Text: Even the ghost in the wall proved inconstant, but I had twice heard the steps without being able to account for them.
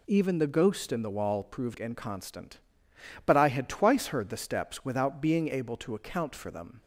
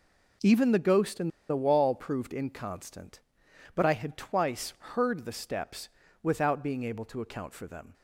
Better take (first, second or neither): first